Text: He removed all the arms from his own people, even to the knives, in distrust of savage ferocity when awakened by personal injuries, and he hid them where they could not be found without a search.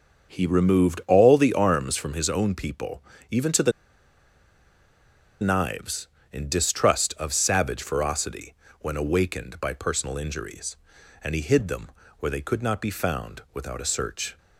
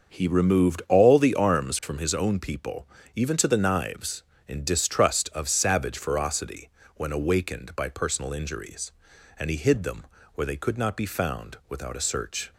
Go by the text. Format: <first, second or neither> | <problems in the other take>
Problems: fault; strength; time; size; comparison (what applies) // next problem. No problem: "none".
second | starts louder than the rest; until 1.3 s; 6.5 dB; also in the second // pauses between "the" and "knives"; strong; at 3.7 s; 1.6 s long // pauses between "ferocity" and "when"; slight; at 8.5 s; 0.26 s long; slight in the second // pauses between "them" and "where"; slight; at 11.9 s; 0.30 s long; slight in the second